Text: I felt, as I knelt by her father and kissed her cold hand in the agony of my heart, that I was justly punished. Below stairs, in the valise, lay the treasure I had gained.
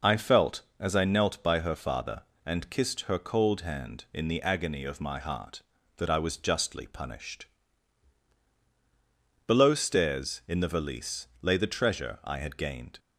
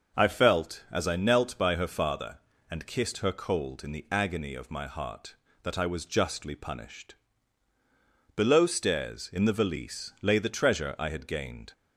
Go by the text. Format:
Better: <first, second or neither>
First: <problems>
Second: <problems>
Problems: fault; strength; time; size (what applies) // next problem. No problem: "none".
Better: first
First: none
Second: skips "hand"; at 3.8 s